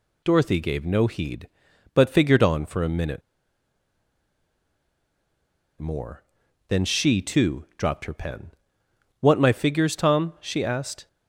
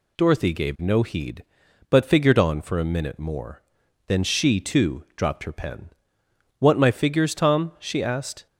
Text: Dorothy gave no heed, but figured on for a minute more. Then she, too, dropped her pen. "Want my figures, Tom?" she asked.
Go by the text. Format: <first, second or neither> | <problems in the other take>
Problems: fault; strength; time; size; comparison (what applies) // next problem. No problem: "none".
second | pauses between "minute" and "more"; strong; at 3.2 s; 2.5 s long